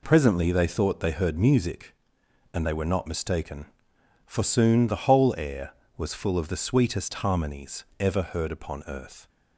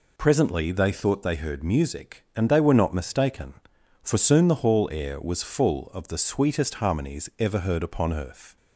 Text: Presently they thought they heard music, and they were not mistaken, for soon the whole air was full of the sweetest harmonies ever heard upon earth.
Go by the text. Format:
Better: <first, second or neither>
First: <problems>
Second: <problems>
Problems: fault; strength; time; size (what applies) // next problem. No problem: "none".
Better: first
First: none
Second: says "hall" for "whole"; at 4.6 s